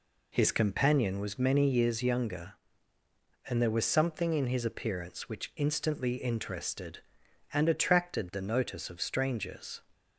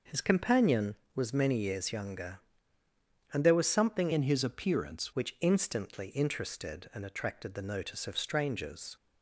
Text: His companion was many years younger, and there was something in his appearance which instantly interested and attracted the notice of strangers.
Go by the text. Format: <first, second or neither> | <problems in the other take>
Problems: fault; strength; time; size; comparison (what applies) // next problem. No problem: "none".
first | changes voice from "in" to "appearance"; from 4.1 to 5.1 s; 1.0 s long